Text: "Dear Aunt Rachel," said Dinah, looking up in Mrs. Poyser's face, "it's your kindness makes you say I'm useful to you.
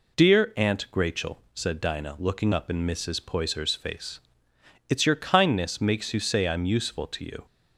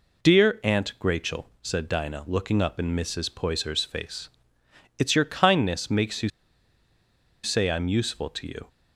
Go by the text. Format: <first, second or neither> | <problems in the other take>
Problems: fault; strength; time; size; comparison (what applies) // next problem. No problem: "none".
first | pauses between "you" and "say"; at 6.2 s; 1.1 s long